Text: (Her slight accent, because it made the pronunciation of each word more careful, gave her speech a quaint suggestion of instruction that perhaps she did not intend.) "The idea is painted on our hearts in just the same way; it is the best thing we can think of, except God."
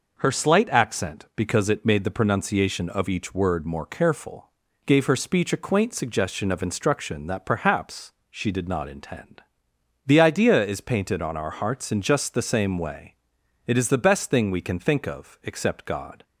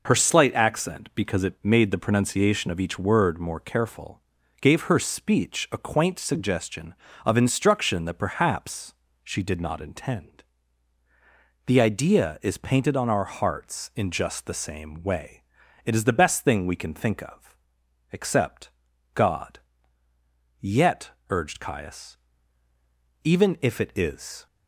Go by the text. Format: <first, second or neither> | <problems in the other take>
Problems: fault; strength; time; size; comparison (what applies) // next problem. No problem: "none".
first | pauses between "perhaps" and "she"; slight; at 8.9 s; 0.30 s long; slight in the first // pauses between "except" and "God"; noticeable; at 18.7 s; 0.46 s long // goes on to say "Yet urged Caius even if it is"; strong; from 20.6 s on; 3.8 s long